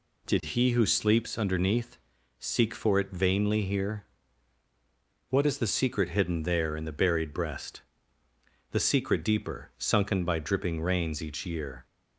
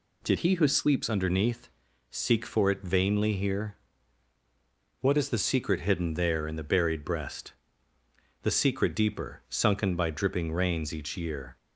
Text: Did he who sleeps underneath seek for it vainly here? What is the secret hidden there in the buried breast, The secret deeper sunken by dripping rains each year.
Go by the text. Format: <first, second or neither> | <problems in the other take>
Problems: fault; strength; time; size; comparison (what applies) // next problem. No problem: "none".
first | changes voice from "he" to "sleeps"; from 0.3 to 1.0 s; 0.7 s long // pauses between "underneath" and "seek"; at 1.6 s; 0.40 s long; also in the first